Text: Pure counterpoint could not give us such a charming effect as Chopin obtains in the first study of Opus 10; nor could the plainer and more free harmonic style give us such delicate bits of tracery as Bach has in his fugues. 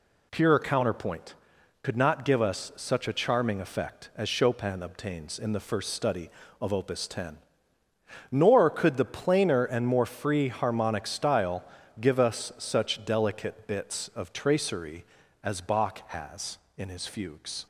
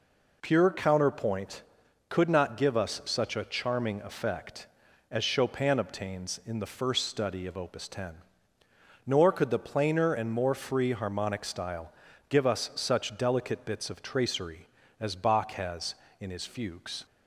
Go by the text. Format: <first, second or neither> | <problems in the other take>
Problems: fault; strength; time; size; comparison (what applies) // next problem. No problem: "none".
neither | pauses between "style" and "give"; slight; the same in both